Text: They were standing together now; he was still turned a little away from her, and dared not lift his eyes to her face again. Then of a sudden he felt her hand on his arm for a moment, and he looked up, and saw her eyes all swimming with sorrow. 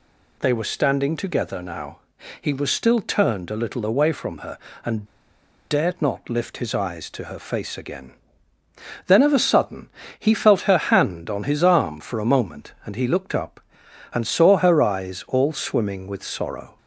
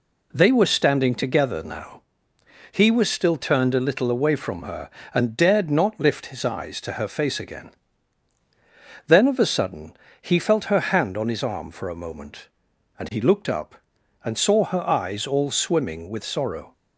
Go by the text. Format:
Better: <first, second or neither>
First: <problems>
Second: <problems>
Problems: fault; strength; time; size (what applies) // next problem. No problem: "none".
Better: second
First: pauses between "and" and "dared"; noticeable; at 5.0 s; 0.65 s long // pauses between "sudden" and "he"; slight; at 9.8 s; 0.30 s long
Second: pauses between "sudden" and "he"; slight; at 9.9 s; 0.28 s long